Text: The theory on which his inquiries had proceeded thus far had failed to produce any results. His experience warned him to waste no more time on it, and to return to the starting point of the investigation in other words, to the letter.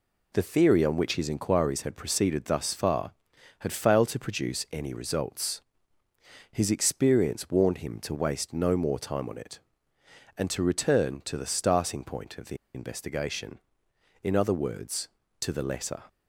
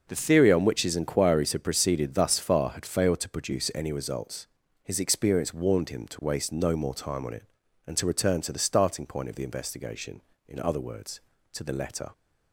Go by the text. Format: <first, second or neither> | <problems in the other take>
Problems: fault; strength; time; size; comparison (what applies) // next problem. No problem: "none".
second | pauses between "the" and "investigation"; slight; at 12.5 s; 0.18 s long